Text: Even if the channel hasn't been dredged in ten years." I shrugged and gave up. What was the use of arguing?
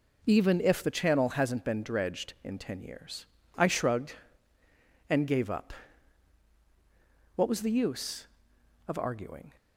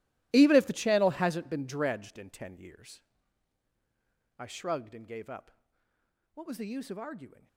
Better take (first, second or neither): first